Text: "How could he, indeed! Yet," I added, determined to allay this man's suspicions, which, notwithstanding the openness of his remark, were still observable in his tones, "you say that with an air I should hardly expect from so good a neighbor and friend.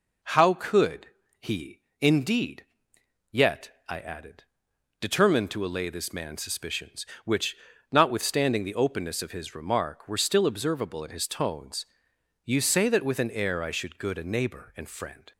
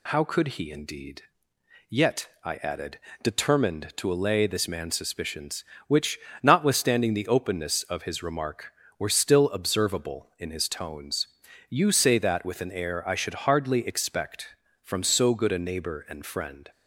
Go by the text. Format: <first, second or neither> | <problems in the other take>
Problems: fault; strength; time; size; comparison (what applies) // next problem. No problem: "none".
second | pauses between "could" and "he"; slight; at 1.0 s; 0.32 s long // skips "hardly expect from so"; at 13.9 s